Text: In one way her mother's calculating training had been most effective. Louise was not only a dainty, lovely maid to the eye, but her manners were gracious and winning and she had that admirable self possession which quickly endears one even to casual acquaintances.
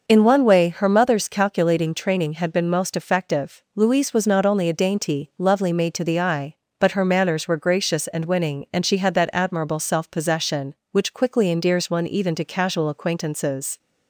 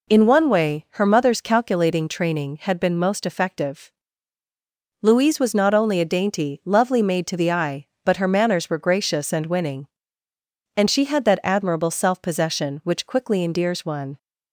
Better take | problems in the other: first | stops before "even to casual acquaintances"; at 14.1 s

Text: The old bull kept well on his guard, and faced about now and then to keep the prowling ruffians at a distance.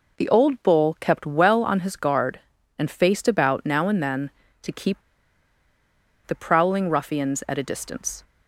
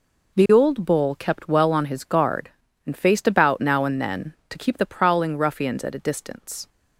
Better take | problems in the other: second | pauses between "keep" and "the"; strong; at 4.9 s; 1.2 s long

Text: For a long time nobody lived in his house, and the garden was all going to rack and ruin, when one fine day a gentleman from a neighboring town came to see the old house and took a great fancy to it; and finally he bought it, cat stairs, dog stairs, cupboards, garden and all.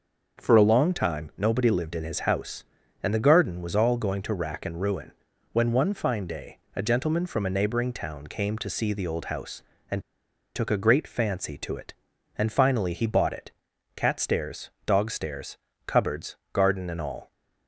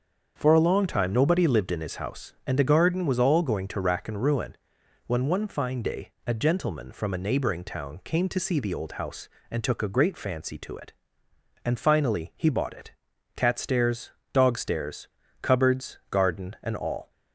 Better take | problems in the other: second | starts louder than the rest; until 1.4 s; 6.5 dB; also in the second // pauses between "day" and "a"; slight; at 6.5 s; 0.16 s long; slight in the second // pauses between "and" and "took"; noticeable; at 10.0 s; 0.55 s long

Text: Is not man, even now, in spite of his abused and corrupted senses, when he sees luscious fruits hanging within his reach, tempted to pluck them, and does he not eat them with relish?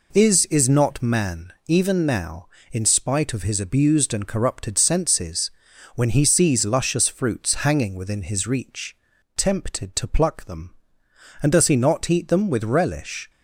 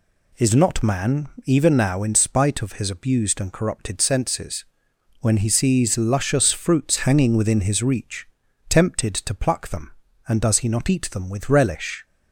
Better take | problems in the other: second | says "Is" twice; at 0.4 s

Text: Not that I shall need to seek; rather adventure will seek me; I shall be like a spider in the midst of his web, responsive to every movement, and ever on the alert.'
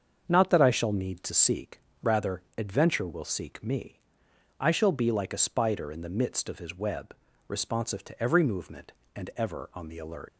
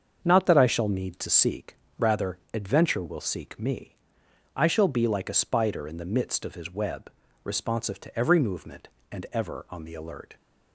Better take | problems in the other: second | starts louder than the rest; until 1.2 s; 7 dB; also in the second // pauses between "rather" and "adventure"; slight; at 2.4 s; 0.16 s long; slight in the second // leaves "alert" unfinished; at 10.2 s; 110 ms

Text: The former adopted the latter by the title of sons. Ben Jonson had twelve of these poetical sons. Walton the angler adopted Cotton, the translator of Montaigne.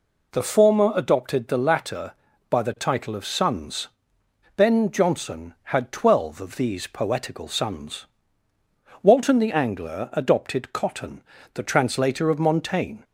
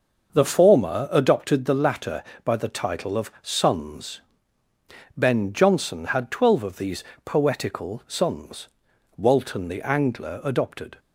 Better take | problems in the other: first | starts louder than the rest; until 1.3 s; 6 dB // pauses between "these" and "poetical"; slight; at 7.0 s; 0.22 s long // stops before "Cotton the translator of Montaigne"; at 10.9 s

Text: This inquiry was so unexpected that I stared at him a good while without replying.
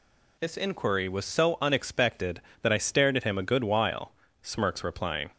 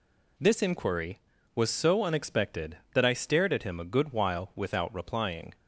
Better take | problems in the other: second | says "smirks" for "without"; at 4.4 s

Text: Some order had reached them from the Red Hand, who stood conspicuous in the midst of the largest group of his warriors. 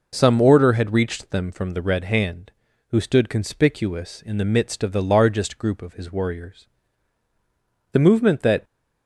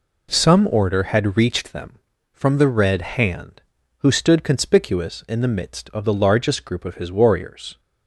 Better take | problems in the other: second | goes on to say "The movement that"; noticeable; from 7.9 s on; 0.70 s long

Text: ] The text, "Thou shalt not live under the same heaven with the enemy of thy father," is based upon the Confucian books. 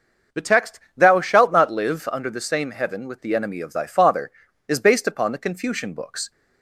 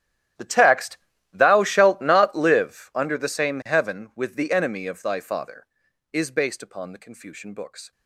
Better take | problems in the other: first | gets quieter; strong; throughout; 19 dB // starts louder than the rest; strong; until 1.7 s; 12 dB; noticeable in the first

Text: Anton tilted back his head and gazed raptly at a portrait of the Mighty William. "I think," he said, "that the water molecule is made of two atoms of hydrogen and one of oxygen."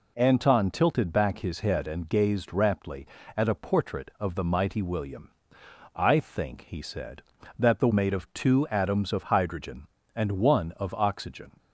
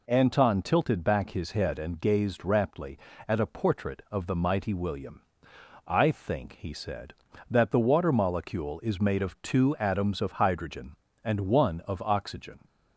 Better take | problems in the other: second | skips "water molecule is"; at 7.9 s

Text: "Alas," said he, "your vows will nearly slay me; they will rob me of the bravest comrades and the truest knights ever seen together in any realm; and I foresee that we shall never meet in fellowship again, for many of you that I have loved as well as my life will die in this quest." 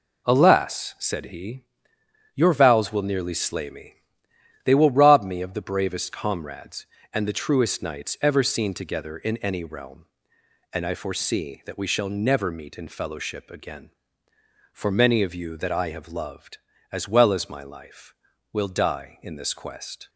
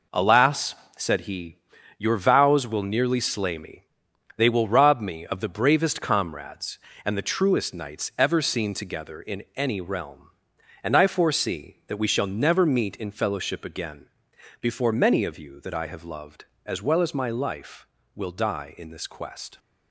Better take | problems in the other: first | says "before" for "for"; at 14.6 s

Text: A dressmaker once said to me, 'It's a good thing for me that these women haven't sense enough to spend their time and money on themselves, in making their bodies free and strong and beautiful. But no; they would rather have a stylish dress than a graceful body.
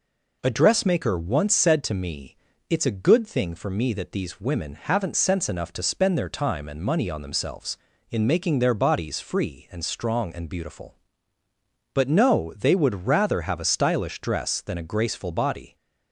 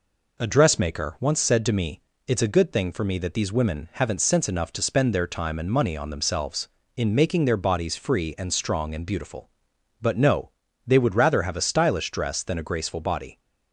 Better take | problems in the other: neither | none

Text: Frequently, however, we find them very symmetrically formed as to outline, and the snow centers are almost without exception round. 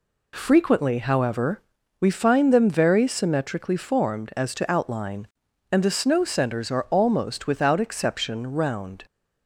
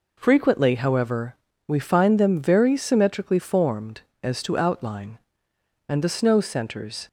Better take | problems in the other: first | stops before "are almost without exception round"; at 7.0 s

